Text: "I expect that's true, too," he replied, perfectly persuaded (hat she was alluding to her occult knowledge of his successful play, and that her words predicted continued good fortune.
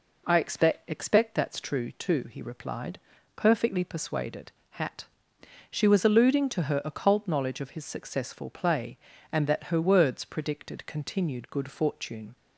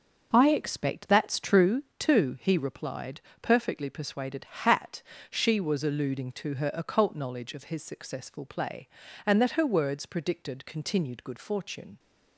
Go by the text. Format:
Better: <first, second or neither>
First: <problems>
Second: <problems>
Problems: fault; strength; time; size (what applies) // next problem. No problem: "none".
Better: second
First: says "expect" twice; at 0.8 s // pauses between "hat" and "she"; noticeable; at 5.0 s; 0.66 s long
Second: pauses between "hat" and "she"; slight; at 5.0 s; 0.28 s long